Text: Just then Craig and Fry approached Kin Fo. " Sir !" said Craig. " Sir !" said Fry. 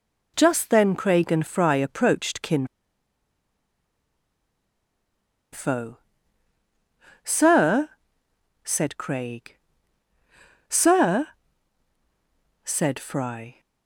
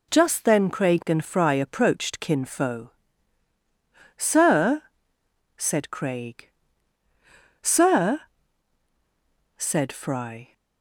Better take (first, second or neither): second